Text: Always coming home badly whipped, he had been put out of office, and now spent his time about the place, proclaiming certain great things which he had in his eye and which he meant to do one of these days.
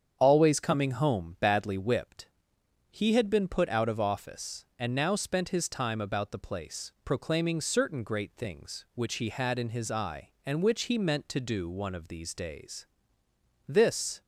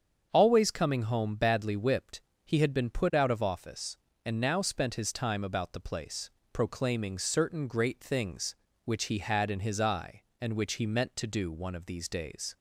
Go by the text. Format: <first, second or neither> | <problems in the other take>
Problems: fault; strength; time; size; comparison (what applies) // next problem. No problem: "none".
second | starts louder than the rest; strong; until 1.2 s; 8 dB; strong in the second // goes on to say "This"; from 13.6 s on; 0.54 s long